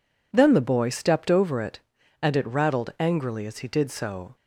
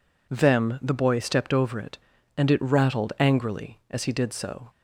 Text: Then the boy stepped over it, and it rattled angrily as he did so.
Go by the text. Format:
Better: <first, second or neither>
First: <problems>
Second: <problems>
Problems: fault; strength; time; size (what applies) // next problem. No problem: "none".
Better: first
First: none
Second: says "Them" for "Then"; at 0.2 s